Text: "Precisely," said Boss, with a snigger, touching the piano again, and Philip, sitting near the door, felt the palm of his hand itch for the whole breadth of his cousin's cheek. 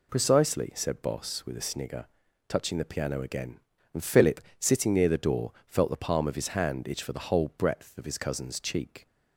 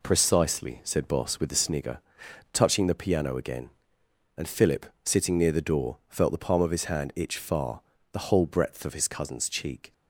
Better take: first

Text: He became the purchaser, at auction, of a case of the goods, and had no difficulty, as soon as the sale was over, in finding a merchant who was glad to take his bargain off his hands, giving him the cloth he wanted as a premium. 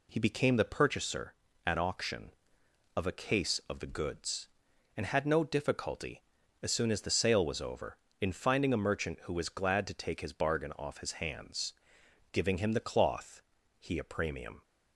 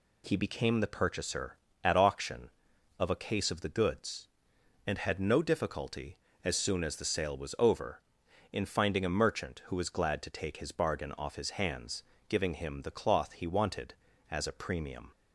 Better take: second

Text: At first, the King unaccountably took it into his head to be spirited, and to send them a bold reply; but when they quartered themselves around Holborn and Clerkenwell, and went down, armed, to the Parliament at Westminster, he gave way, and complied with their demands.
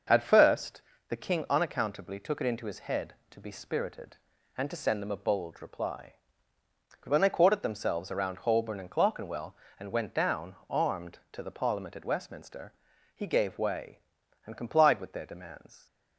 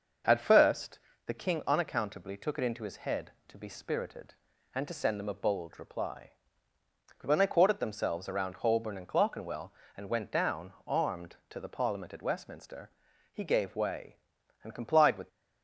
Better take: first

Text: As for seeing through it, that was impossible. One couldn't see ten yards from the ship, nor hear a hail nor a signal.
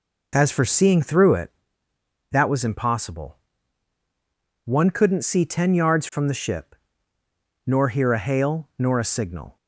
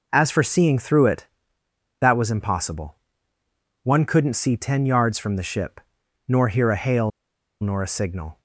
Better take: first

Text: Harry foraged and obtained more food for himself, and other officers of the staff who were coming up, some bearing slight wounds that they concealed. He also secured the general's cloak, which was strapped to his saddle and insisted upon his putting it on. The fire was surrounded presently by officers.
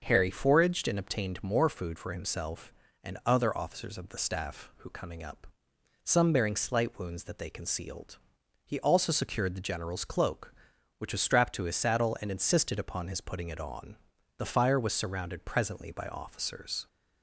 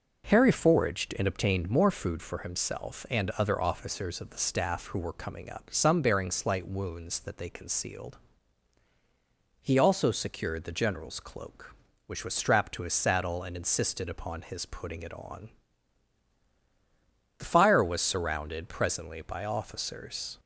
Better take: second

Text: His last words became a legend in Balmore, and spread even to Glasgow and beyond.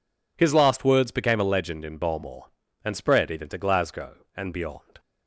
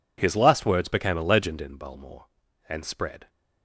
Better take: first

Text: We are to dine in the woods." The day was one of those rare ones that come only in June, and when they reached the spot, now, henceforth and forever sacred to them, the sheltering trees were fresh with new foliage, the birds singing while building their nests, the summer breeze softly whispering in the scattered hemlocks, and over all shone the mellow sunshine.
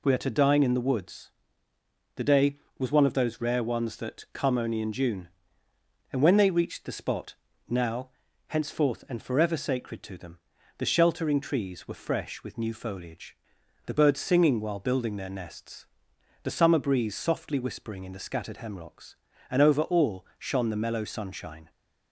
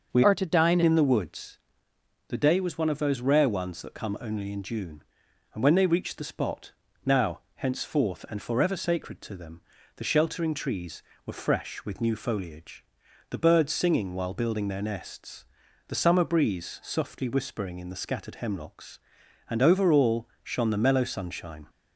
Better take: first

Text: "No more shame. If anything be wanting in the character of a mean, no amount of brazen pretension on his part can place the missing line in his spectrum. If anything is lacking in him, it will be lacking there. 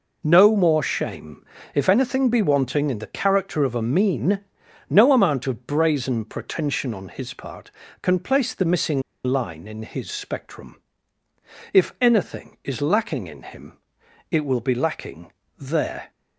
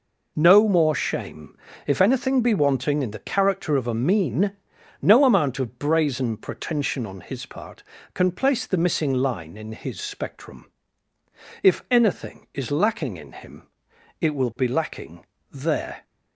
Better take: second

